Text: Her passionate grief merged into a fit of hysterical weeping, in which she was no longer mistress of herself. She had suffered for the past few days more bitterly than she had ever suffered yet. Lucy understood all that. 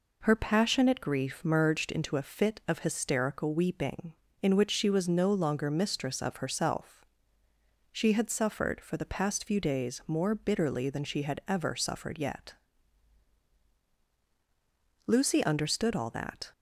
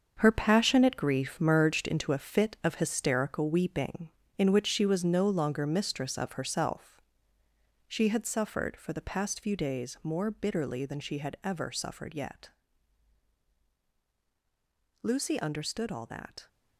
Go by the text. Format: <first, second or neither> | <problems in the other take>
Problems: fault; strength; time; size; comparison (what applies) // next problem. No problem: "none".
first | gets quieter; strong; throughout; 9.5 dB